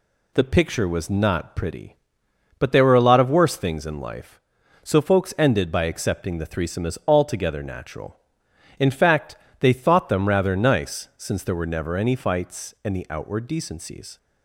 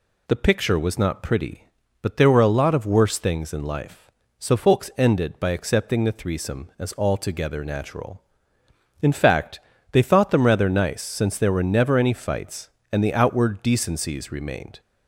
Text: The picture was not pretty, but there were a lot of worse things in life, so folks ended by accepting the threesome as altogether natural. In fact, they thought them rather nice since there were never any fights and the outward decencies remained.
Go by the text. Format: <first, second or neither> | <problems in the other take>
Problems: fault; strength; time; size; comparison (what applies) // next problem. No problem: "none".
second | stops before "remained"; at 14.1 s